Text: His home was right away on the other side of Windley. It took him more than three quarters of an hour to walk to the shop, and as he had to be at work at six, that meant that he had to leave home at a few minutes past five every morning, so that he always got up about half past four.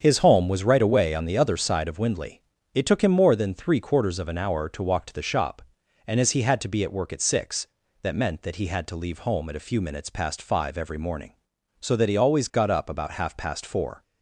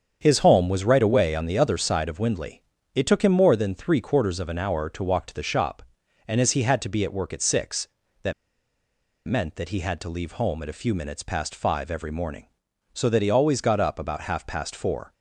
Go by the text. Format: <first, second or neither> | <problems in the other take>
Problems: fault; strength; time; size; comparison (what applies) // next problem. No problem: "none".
first | starts louder than the rest; strong; until 1.2 s; 7.5 dB; strong in the first // pauses between "that" and "meant"; noticeable; at 8.3 s; 0.95 s long